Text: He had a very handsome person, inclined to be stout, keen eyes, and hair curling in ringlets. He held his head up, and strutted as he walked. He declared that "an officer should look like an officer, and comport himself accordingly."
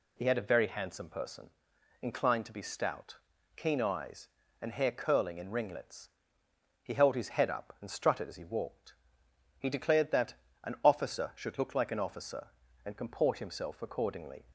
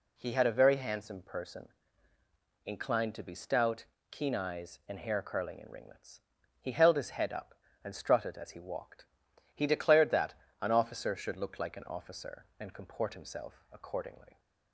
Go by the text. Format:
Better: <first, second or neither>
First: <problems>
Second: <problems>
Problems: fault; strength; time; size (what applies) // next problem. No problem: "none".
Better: neither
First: pauses between "that" and "an"; slight; at 10.3 s; 0.30 s long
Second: pauses between "that" and "an"; slight; at 10.3 s; 0.26 s long